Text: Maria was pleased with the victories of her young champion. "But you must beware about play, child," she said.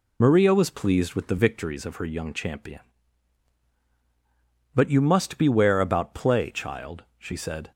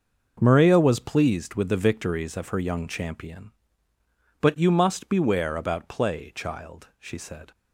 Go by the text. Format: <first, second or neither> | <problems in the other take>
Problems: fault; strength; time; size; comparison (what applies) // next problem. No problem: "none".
second | loses the start of "Maria"; at 0.2 s; 50 ms